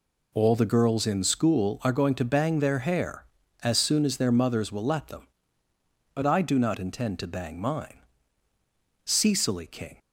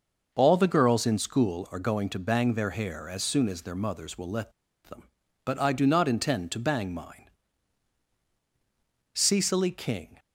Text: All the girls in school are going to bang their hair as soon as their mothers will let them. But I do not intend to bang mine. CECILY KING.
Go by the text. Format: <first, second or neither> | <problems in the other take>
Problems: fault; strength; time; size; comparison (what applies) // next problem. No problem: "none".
first | pauses between "let" and "them"; slight; at 4.5 s; 0.33 s long